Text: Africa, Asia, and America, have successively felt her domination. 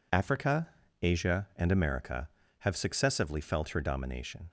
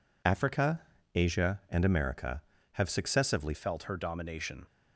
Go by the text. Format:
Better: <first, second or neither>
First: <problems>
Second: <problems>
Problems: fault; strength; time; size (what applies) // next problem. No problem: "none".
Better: first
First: none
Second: changes voice at "felt"; from 3.5 s on; 1.1 s long